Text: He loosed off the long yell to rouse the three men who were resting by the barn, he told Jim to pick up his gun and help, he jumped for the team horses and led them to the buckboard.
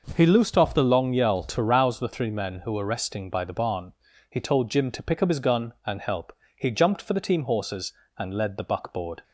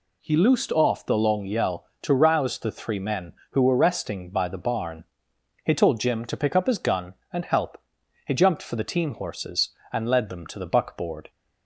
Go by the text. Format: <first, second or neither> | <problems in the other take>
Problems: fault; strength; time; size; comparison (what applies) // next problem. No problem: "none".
second | skips "them to"; at 8.5 s